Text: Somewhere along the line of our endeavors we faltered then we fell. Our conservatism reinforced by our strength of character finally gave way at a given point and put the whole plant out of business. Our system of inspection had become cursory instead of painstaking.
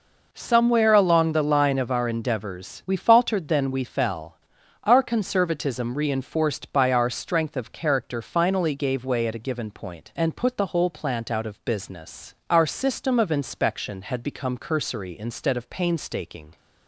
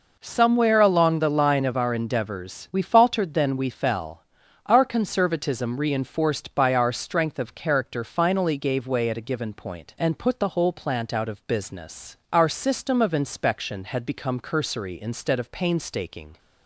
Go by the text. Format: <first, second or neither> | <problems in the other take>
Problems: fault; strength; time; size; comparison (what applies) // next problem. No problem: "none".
neither | none